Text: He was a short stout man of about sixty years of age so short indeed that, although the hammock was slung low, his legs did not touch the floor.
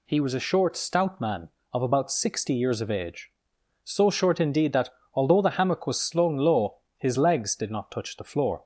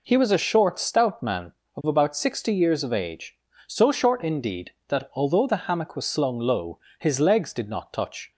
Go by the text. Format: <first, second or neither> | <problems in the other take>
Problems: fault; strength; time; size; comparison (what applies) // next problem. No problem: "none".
first | stops before "the floor"; at 8.3 s